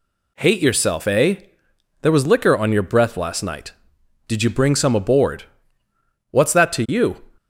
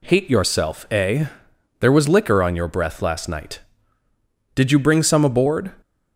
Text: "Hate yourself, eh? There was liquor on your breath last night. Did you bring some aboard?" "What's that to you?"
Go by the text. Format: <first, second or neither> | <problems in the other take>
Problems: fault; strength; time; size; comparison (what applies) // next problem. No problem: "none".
first | stops before "What's that to you"; at 5.8 s